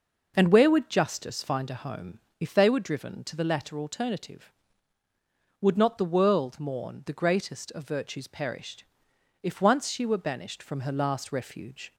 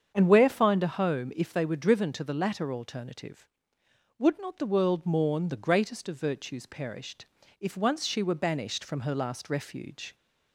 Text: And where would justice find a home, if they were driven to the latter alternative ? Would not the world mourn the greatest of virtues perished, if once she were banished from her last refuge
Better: first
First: none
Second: starts louder than the rest; strong; until 1.1 s; 7.5 dB // skips "would justice"; at 0.4 s

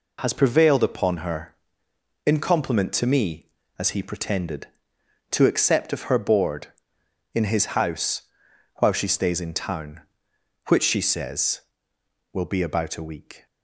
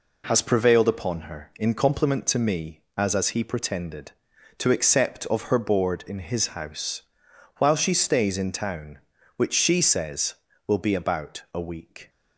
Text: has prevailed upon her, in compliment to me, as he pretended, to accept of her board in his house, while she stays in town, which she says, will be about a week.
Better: first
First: none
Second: says "as" twice; at 3.1 s

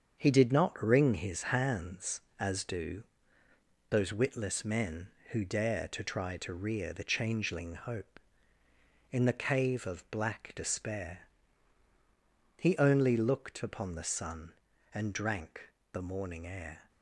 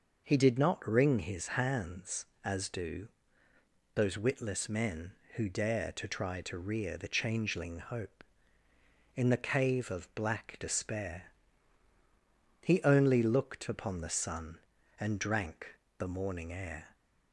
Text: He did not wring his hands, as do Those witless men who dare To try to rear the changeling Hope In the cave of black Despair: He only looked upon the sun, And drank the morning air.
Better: second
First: gets quieter; throughout; 6.5 dB // pauses between "do" and "Those"; noticeable; at 3.0 s; 0.86 s long // pauses between "drank" and "the"; slight; at 15.7 s; 0.22 s long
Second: pauses between "do" and "Those"; noticeable; at 3.0 s; 0.86 s long // pauses between "drank" and "the"; slight; at 15.7 s; 0.22 s long

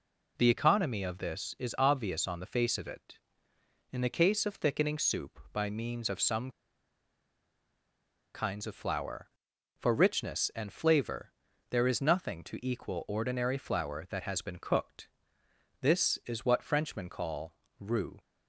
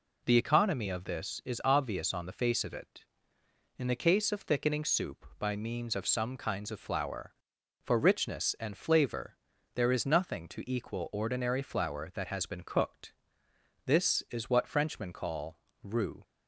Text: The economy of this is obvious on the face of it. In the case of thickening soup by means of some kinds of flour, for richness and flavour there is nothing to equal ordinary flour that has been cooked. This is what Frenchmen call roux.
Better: second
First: pauses between "some" and "kinds"; strong; at 6.5 s; 1.8 s long // pauses between "flavour" and "there"; at 11.3 s; 0.38 s long // pauses between "call" and "roux"; slight; at 17.5 s; 0.26 s long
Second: pauses between "flavour" and "there"; at 9.3 s; 0.38 s long // pauses between "call" and "roux"; slight; at 15.5 s; 0.26 s long

